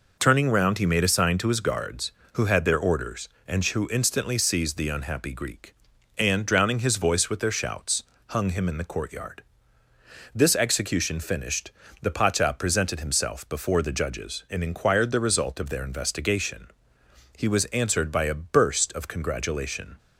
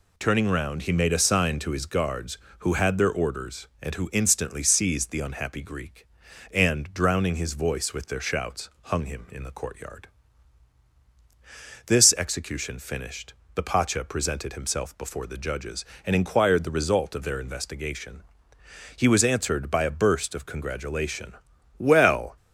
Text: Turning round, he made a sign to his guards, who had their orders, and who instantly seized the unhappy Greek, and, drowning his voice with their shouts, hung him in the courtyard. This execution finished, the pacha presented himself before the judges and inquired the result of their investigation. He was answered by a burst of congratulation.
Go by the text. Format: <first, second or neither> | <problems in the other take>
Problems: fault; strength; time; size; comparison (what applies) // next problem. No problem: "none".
first | goes on to say "Well"; from 21.7 s on; 0.58 s long